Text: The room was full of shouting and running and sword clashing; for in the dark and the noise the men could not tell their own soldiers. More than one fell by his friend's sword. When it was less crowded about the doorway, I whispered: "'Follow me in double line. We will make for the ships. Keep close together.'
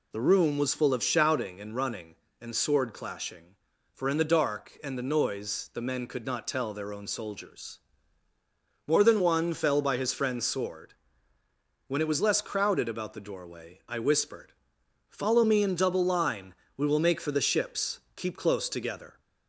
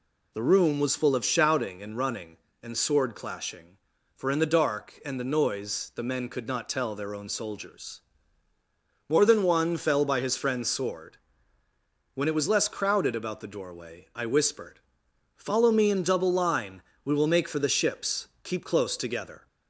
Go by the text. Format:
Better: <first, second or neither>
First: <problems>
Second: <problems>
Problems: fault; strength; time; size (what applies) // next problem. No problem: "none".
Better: neither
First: none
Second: none